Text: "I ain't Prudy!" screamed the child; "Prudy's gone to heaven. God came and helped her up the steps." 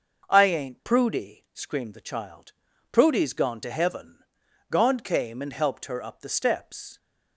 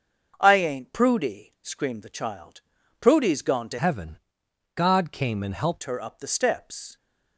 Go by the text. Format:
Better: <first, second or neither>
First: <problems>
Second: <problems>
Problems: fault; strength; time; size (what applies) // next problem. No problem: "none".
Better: first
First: none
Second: starts louder than the rest; until 1.4 s; 6.5 dB // changes voice from "heaven" to "helped"; from 3.7 to 5.8 s; 2.1 s long